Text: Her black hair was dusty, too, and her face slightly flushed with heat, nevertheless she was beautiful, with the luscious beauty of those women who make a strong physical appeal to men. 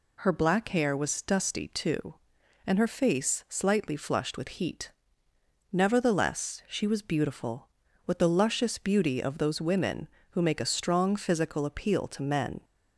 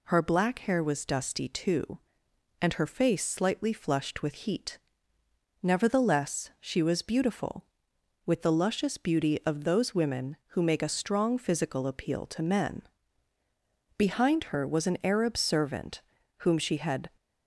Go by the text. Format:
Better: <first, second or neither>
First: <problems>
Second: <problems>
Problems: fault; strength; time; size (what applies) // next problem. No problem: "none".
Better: first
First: none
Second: goes on to say "Behind her was an Arab servant whom she had"; strong; from 13.9 s on; 3.1 s long